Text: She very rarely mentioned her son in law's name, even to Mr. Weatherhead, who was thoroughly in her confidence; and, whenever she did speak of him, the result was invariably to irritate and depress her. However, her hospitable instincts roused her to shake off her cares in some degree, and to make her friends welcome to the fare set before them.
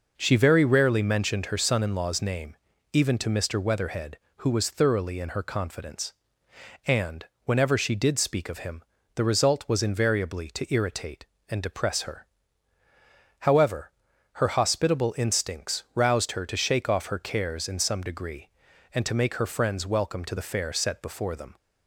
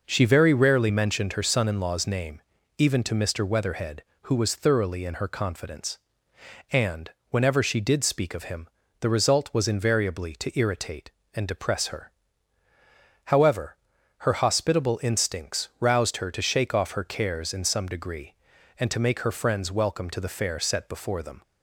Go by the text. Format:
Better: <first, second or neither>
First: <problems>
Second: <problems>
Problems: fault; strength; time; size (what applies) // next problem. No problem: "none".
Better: neither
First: none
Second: none